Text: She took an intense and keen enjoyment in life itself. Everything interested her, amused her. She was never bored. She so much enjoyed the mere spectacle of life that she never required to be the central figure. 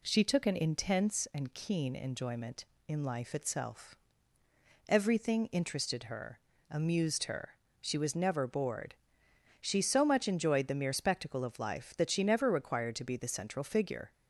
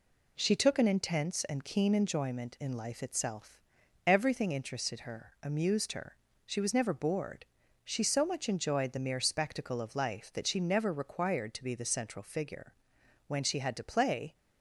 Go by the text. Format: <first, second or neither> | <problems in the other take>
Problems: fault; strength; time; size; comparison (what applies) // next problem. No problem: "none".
first | goes on to say "When she had to play"; noticeable; from 13.2 s on; 1.0 s long